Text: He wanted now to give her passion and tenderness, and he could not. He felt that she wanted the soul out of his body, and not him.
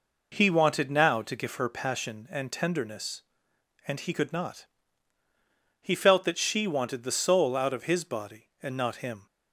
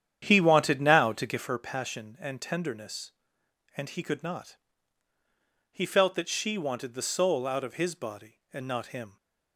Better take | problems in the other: first | starts louder than the rest; strong; until 1.6 s; 9.5 dB

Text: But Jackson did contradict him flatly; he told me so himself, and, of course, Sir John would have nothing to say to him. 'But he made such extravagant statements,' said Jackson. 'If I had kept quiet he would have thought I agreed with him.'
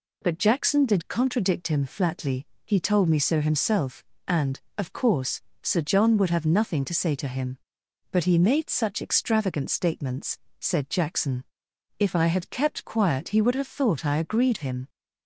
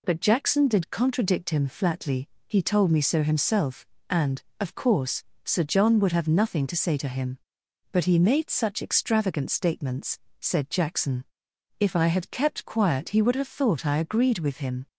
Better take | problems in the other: second | skips "with"; at 14.5 s

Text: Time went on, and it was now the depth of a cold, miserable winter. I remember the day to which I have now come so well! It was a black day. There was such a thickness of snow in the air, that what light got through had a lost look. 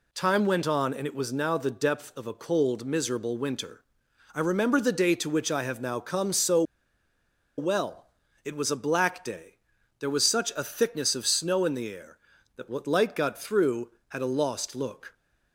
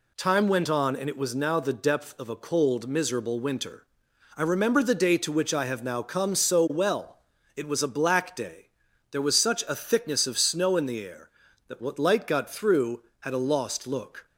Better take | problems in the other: second | pauses between "so" and "well"; noticeable; at 6.6 s; 0.94 s long

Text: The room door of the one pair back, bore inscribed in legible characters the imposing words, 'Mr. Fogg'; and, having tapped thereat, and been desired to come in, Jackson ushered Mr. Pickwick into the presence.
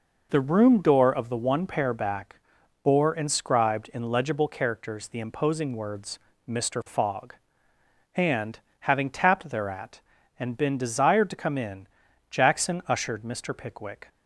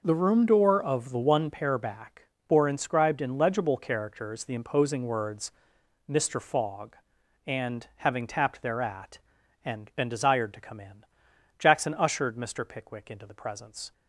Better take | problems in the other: second | stops before "into the presence"; at 14.0 s

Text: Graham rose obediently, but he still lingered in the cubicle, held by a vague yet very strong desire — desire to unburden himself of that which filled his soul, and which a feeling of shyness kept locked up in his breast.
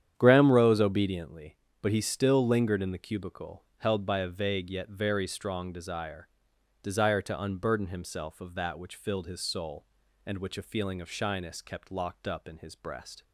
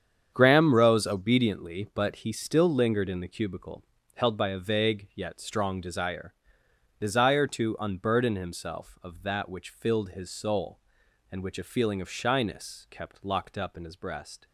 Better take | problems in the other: first | starts louder than the rest; strong; until 1.3 s; 8 dB; strong in the first // skips "very"; at 5.3 s

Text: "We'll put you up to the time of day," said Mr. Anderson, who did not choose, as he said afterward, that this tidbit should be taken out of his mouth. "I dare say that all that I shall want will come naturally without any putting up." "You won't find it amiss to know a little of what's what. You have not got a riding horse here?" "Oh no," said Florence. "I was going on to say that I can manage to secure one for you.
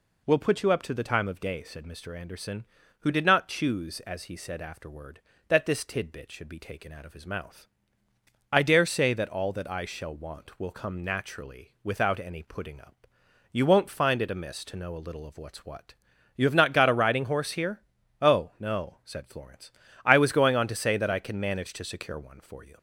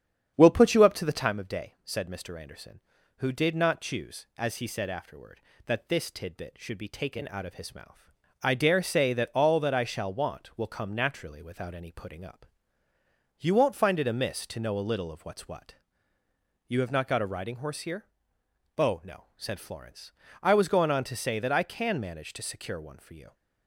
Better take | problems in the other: first | starts louder than the rest; strong; until 1.3 s; 8.5 dB

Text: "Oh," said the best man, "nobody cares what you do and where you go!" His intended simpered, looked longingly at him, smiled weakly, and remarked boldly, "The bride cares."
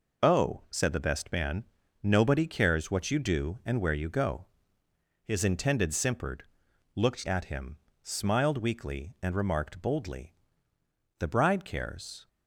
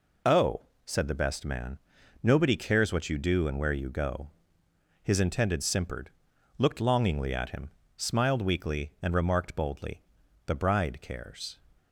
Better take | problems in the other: second | skips "longingly"; at 7.2 s

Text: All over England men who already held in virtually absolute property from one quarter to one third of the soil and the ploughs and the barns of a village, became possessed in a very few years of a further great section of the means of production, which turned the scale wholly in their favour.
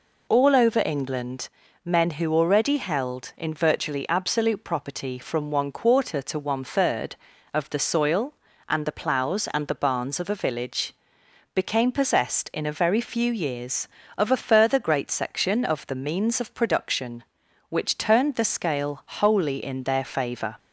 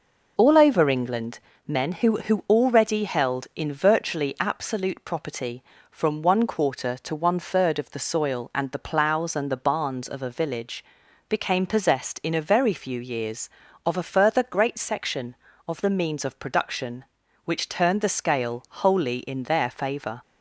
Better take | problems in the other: first | pauses between "England" and "men"; slight; at 1.3 s; 0.28 s long; also in the first // says "who" twice; at 2.2 s

